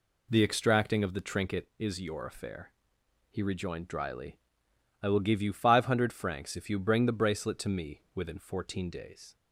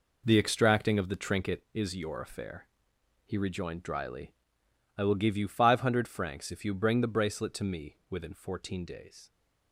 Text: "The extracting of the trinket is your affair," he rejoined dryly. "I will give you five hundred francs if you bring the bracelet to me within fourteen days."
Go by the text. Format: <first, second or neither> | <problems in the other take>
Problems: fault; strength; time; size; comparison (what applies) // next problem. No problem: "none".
first | gets quieter; strong; throughout; 9.5 dB